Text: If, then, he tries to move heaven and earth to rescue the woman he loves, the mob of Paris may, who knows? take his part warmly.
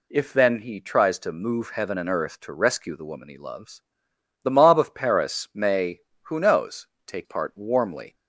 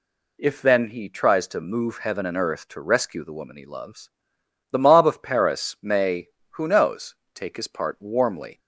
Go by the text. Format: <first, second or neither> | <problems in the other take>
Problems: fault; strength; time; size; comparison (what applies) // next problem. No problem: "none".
second | skips "his"; at 7.2 s